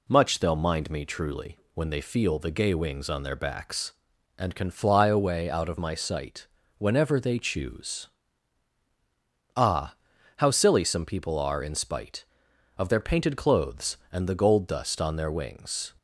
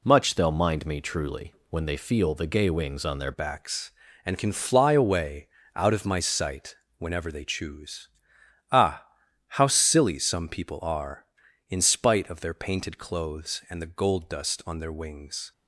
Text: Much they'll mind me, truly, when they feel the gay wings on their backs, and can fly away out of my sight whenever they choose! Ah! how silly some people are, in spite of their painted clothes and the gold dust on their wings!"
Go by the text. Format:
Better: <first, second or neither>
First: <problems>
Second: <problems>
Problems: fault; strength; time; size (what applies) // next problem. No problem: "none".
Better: first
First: pauses between "sight" and "whenever"; slight; at 6.4 s; 0.32 s long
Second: changes voice at "backs"; from 3.3 s on; 12.2 s long // pauses between "away" and "out"; slight; at 5.4 s; 0.28 s long // pauses between "sight" and "whenever"; slight; at 6.7 s; 0.22 s long